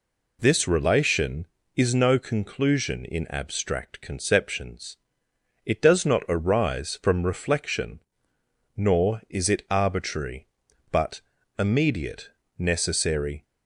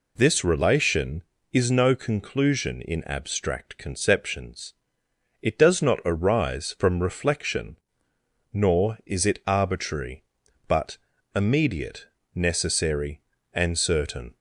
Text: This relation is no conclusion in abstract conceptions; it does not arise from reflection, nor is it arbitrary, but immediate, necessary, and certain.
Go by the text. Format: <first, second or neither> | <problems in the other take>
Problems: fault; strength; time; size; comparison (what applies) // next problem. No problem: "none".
second | pauses between "but" and "immediate"; at 11.1 s; 0.38 s long; also in the second // stops before "and certain"; at 13.4 s